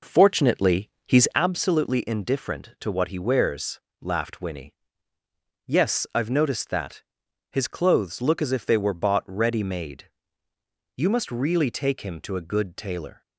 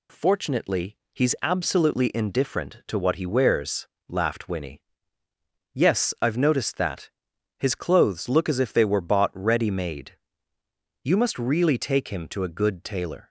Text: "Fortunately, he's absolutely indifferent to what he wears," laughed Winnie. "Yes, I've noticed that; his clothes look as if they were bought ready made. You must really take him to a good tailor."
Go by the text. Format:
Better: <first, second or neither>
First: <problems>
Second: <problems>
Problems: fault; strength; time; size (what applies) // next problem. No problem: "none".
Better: second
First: starts louder than the rest; noticeable; until 1.5 s; 4.5 dB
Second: none